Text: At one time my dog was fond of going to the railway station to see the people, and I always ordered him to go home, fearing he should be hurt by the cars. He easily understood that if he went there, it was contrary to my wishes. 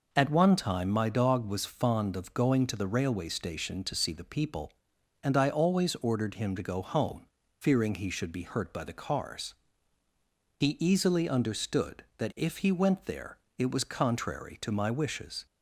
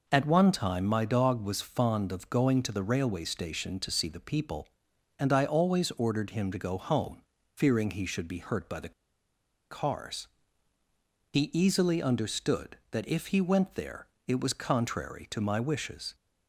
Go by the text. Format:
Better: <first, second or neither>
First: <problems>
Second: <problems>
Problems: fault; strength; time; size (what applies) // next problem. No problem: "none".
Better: first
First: none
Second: pauses between "the" and "cars"; noticeable; at 8.9 s; 0.78 s long